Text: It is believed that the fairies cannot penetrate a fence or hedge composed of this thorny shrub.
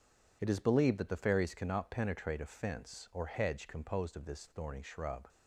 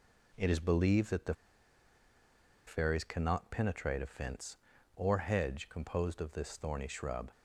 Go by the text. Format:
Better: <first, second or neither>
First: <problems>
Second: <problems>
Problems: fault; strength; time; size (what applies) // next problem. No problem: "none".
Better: first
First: none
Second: pauses between "the" and "fairies"; strong; at 1.3 s; 1.3 s long